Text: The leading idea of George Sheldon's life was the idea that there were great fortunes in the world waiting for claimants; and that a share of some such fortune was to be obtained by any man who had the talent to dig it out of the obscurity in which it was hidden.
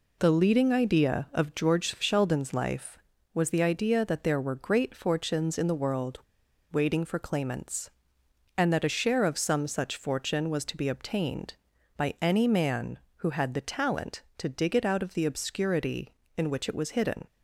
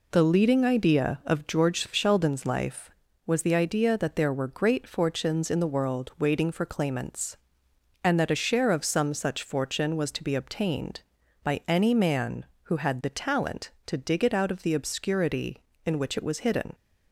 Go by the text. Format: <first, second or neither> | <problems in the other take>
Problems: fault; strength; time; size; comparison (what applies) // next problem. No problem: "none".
second | pauses between "world" and "waiting"; noticeable; at 6.2 s; 0.49 s long